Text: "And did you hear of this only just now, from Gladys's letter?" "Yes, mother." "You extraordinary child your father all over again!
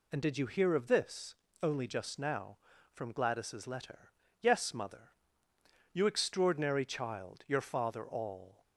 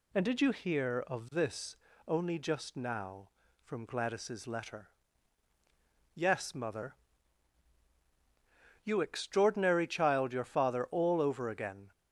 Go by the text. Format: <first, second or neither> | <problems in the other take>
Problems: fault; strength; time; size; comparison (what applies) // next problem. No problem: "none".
second | pauses between "this" and "only"; slight; at 1.3 s; 0.28 s long; slight in the second // stops before "over again"; at 8.6 s